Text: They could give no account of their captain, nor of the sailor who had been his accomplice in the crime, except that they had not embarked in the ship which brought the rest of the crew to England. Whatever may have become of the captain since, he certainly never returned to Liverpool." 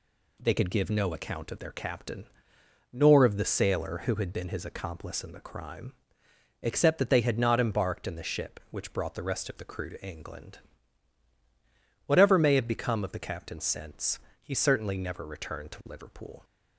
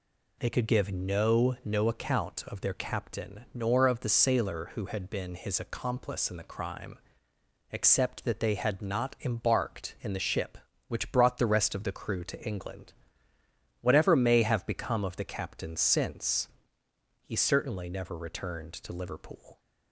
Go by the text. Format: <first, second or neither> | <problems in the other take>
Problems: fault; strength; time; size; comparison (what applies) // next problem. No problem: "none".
first | says "no" twice; at 1.6 s